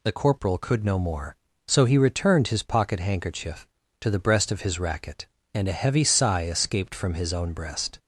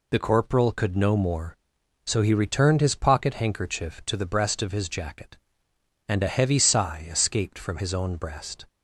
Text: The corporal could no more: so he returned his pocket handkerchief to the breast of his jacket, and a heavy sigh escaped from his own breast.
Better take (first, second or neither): second